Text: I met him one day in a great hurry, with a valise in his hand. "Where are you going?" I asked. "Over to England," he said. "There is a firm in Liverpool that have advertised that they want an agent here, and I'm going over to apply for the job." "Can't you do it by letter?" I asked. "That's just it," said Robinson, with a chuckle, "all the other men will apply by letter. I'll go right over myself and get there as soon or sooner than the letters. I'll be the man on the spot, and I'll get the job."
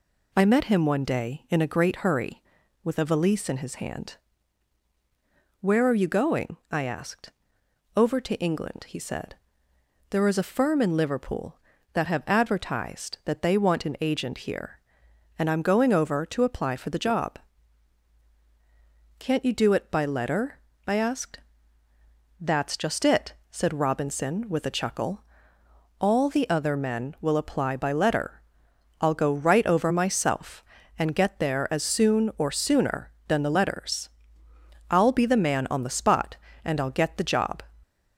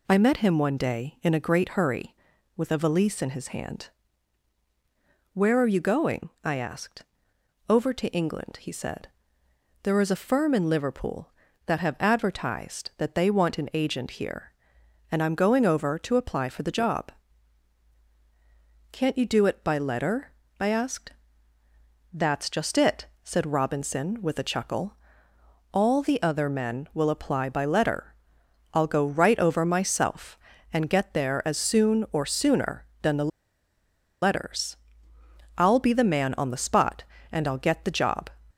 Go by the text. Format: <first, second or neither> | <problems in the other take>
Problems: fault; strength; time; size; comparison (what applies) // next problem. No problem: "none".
first | pauses between "the" and "letters"; noticeable; at 33.3 s; 0.92 s long